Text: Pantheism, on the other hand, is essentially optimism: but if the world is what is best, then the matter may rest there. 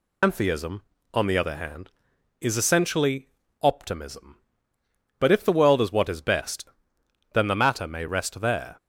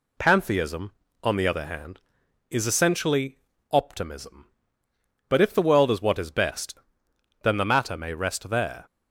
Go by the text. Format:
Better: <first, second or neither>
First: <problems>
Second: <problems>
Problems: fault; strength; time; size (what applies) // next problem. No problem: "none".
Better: second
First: loses the start of "Pantheism"; at 0.2 s; 135 ms // pauses between "essentially" and "optimism"; slight; at 3.2 s; 0.34 s long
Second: pauses between "essentially" and "optimism"; slight; at 3.3 s; 0.34 s long